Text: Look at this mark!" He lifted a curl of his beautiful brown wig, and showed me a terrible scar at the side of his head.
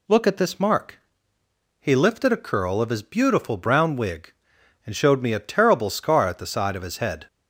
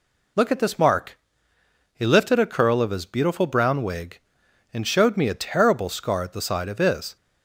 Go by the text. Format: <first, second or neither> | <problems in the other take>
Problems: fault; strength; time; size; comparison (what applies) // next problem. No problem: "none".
first | stops before "head"; at 7.1 s